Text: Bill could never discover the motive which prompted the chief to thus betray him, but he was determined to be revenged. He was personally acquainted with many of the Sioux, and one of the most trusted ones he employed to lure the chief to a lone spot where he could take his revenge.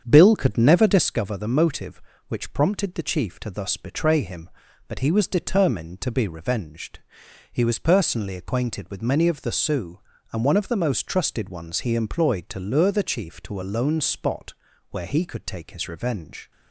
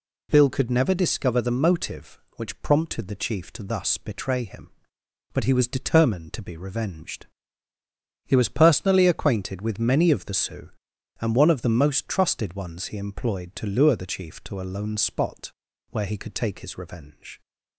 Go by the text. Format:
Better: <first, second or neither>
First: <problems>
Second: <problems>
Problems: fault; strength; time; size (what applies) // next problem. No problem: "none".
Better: second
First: starts louder than the rest; strong; until 1.1 s; 7.5 dB // pauses between "spot" and "where"; slight; at 14.5 s; 0.36 s long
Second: pauses between "spot" and "where"; at 15.5 s; 0.40 s long